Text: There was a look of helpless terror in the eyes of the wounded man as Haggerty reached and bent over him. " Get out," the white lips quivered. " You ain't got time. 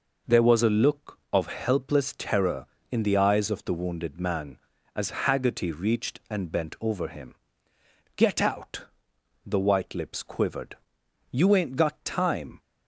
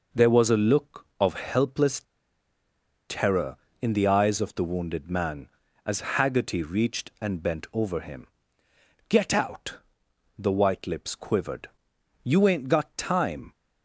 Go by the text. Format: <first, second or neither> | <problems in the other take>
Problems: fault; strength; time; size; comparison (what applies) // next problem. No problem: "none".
first | pauses between "helpless" and "terror"; at 2.0 s; 1.0 s long